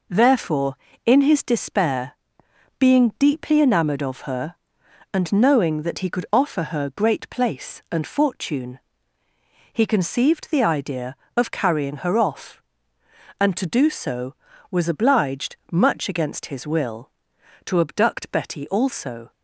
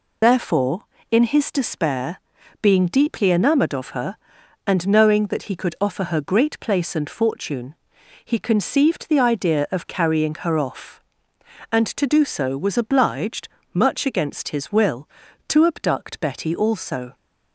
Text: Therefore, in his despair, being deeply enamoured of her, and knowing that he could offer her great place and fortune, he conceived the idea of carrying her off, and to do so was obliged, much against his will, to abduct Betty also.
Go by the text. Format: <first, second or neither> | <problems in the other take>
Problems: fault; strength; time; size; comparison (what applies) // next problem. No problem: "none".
first | loses the start of "Therefore"; at 0.2 s; 90 ms